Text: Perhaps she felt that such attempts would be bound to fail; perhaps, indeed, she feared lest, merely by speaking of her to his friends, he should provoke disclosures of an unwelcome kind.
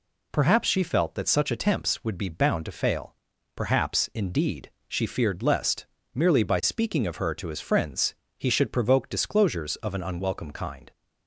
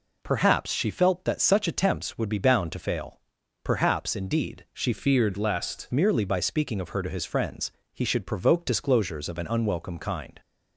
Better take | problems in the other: first | changes voice from "feared" to "lest"; from 4.9 to 5.8 s; 0.9 s long

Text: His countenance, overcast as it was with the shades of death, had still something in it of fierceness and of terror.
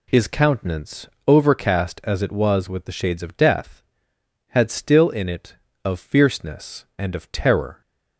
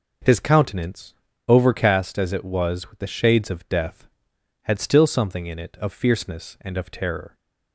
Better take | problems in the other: second | skips "something"; at 5.1 s

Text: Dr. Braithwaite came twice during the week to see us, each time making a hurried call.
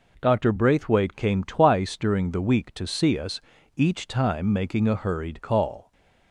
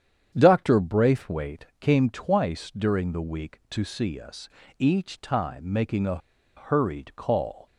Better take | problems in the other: first | starts louder than the rest; strong; until 1.3 s; 8.5 dB // pauses between "a" and "hurried"; at 6.1 s; 0.39 s long

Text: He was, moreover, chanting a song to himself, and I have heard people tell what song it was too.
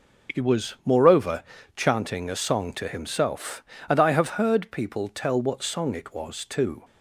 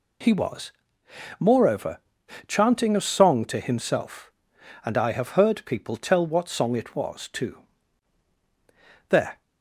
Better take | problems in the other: first | goes on to say "There"; slight; from 9.0 s on; 0.32 s long

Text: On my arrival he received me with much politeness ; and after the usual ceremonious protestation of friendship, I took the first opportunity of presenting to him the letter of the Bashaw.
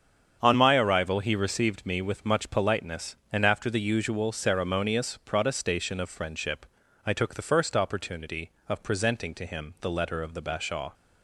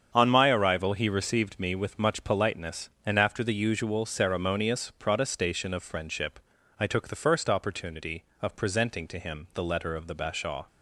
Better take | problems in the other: neither | starts louder than the rest; strong; the same in both

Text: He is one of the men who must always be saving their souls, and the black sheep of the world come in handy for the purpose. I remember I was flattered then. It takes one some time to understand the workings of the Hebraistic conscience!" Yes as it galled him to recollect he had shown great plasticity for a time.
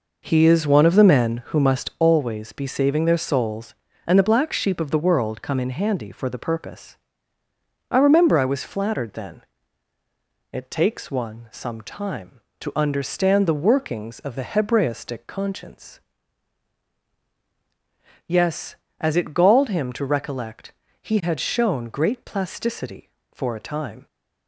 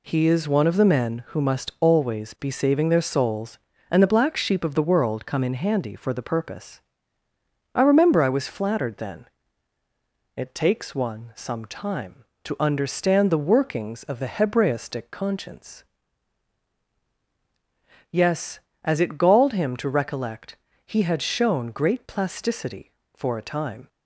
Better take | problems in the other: second | starts louder than the rest; noticeable; until 2.0 s; 5 dB // pauses between "recollect" and "he"; slight; at 20.7 s; 0.30 s long; slight in the second

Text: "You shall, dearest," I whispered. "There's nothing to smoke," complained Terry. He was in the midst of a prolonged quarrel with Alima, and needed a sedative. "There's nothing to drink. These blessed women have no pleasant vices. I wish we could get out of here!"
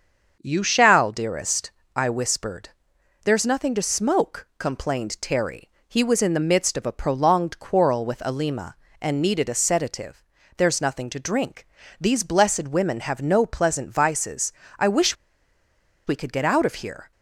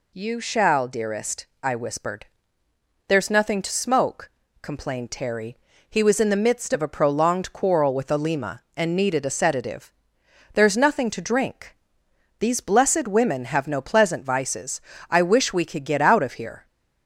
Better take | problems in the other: second | starts louder than the rest; until 1.4 s; 6.5 dB // pauses between "wish" and "we"; noticeable; at 15.1 s; 0.91 s long

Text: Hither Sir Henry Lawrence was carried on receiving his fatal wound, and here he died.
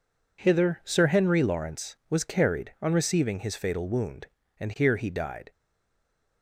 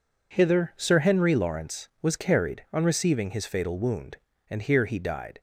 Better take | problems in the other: second | stays silent after the last word; slight; from 5.5 s on; 0.9 s long

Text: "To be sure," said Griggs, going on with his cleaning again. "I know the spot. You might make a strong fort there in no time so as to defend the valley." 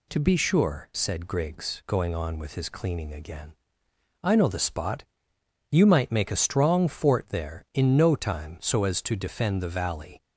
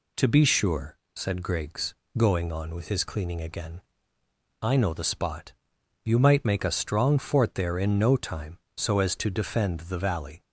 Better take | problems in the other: neither | none

